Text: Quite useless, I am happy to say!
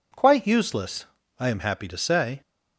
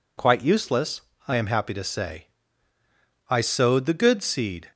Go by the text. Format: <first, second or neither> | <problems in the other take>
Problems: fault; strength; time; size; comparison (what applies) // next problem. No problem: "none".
first | goes on to say "I sowed the good seed"; from 3.2 s on; 1.4 s long